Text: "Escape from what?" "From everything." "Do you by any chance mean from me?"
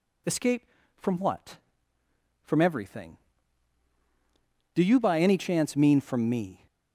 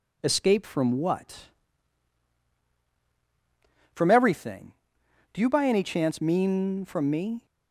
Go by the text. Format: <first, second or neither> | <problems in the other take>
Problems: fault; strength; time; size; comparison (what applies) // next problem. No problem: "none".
neither | none